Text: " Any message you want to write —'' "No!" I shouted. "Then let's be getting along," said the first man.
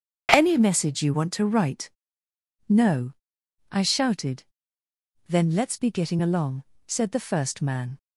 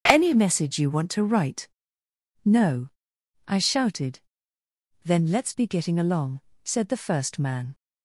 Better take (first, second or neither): neither